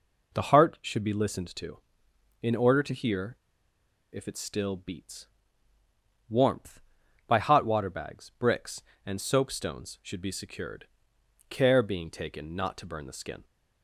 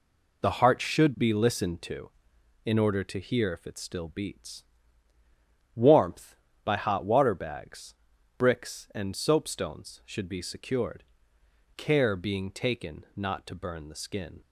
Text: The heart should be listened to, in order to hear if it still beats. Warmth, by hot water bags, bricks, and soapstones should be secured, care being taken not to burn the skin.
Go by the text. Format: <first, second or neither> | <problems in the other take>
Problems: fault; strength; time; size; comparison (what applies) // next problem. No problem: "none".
second | pauses between "hear" and "if"; noticeable; at 3.3 s; 0.76 s long